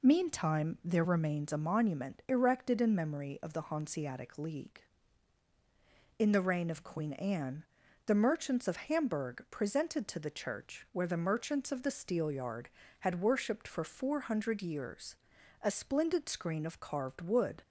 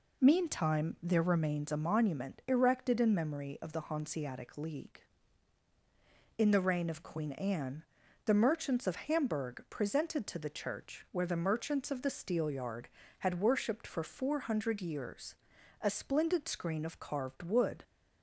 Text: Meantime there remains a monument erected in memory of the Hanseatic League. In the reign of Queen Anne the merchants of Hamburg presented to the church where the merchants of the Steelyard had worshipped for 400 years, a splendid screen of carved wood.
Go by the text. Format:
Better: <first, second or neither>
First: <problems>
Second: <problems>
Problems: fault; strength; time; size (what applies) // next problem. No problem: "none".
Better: neither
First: pauses between "Anne" and "the"; at 7.6 s; 0.42 s long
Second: pauses between "Anne" and "the"; at 7.8 s; 0.42 s long